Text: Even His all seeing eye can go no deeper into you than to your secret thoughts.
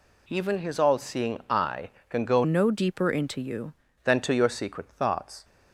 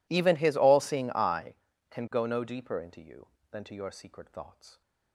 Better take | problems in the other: second | changes voice from "no" to "you"; from 2.4 to 3.7 s; 1.3 s long

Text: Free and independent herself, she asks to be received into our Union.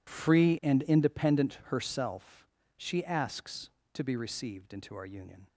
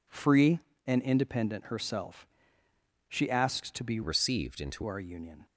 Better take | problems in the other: first | changes voice from "received" to "into"; from 4.0 to 4.8 s; 0.8 s long

